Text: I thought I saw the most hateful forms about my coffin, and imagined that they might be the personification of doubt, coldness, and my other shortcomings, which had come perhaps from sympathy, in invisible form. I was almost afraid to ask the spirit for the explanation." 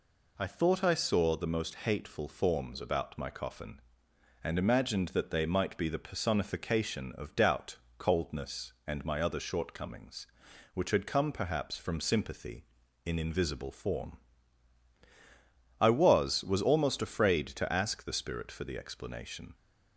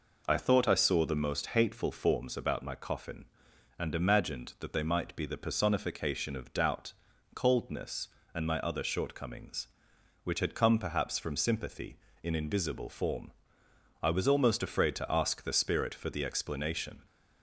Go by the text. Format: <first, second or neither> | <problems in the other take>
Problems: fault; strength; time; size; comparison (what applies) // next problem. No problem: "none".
second | says "was" twice; at 16.4 s